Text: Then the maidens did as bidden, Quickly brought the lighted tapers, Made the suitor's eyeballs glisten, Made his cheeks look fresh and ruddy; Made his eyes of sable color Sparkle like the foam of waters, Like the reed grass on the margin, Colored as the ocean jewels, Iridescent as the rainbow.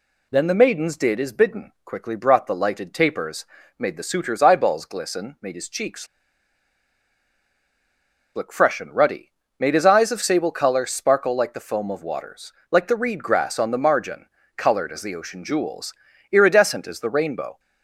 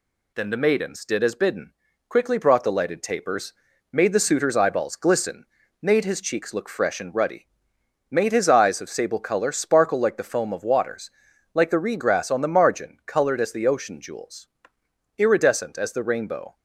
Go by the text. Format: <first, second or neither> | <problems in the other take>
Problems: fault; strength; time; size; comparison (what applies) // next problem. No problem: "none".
second | pauses between "cheeks" and "look"; strong; at 6.0 s; 2.2 s long